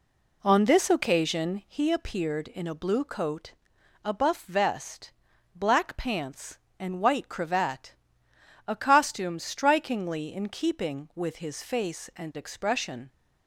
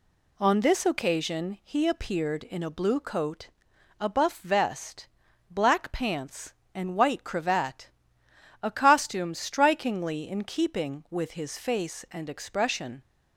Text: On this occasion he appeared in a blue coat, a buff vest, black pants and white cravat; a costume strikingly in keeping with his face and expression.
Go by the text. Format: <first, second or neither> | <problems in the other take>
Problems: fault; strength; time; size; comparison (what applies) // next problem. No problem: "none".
second | starts louder than the rest; slight; until 1.9 s; 2.5 dB